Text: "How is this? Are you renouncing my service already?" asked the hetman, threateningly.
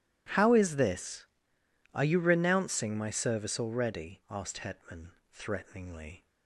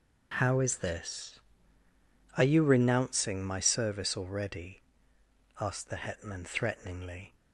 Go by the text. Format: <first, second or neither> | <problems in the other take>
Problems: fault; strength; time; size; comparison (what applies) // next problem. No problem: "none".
second | skips "the"; at 4.5 s